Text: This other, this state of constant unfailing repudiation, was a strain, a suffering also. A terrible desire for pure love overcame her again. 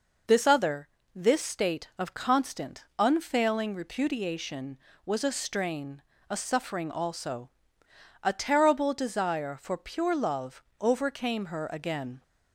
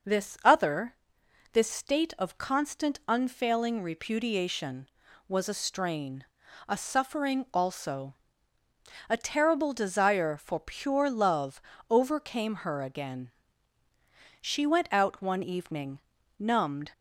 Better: first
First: pauses between "love" and "overcame"; slight; at 10.6 s; 0.18 s long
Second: pauses between "love" and "overcame"; slight; at 11.6 s; 0.26 s long // goes on to say "She went out one evening numbed"; strong; from 14.4 s on; 2.5 s long

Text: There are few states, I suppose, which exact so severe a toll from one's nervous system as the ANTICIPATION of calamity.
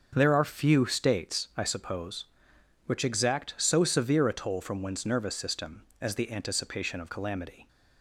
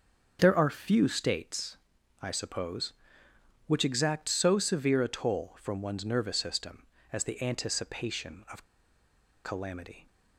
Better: first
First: starts louder than the rest; until 1.1 s; 7 dB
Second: starts louder than the rest; until 1.4 s; 7 dB // pauses between "of" and "calamity"; noticeable; at 8.6 s; 0.82 s long

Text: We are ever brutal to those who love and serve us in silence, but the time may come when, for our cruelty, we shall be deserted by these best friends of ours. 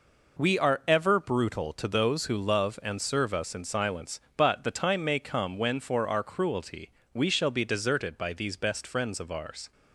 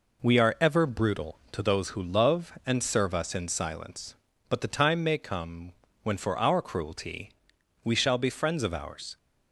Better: first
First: none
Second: pauses between "come" and "when"; slight; at 5.7 s; 0.32 s long // skips "deserted by these best"; at 8.2 s

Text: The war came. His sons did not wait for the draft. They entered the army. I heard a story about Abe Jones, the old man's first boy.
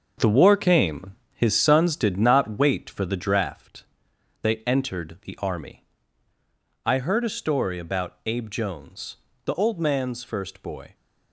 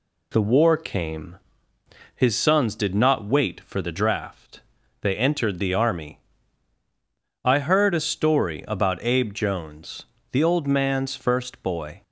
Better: second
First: gets quieter; strong; throughout; 7.5 dB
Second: none

